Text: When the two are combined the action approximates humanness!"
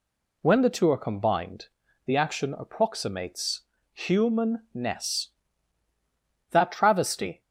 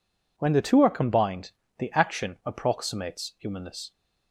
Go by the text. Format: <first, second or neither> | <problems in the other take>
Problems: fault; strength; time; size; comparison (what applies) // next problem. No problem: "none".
second | pauses between "combined" and "the"; at 1.6 s; 0.40 s long; slight in the second // pauses between "approximates" and "humanness"; slight; at 3.6 s; 0.32 s long // goes on to say "That travesty"; noticeable; from 6.5 s on; 0.90 s long